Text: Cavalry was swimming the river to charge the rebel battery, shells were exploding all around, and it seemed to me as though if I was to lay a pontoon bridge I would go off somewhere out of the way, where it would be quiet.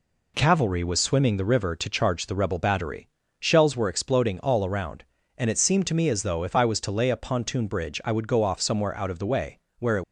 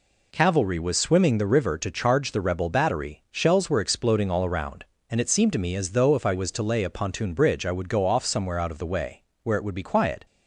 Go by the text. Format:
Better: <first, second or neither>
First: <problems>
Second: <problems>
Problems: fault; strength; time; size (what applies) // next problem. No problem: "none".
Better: second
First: stops before "would be quiet"; at 10.0 s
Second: none